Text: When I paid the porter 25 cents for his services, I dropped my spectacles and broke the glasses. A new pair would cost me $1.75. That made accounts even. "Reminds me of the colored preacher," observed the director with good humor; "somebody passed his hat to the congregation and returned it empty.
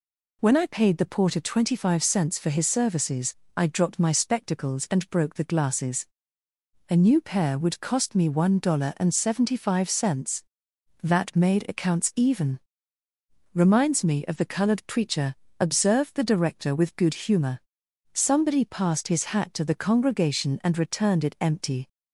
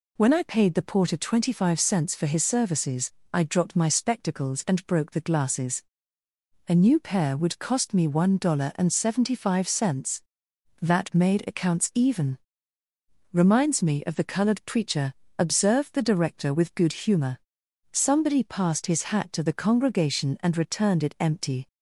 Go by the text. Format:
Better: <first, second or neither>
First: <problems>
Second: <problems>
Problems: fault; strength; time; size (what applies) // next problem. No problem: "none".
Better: neither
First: none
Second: none